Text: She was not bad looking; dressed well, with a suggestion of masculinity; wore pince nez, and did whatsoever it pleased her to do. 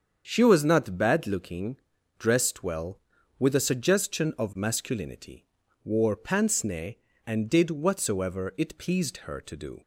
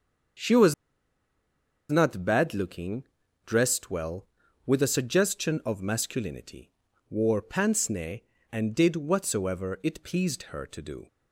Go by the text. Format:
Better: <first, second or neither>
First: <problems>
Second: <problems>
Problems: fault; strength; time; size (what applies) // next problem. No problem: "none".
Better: first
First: starts louder than the rest; strong; until 1.2 s; 7 dB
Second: starts louder than the rest; strong; until 2.5 s; 7 dB // pauses between "was" and "not"; at 0.7 s; 1.1 s long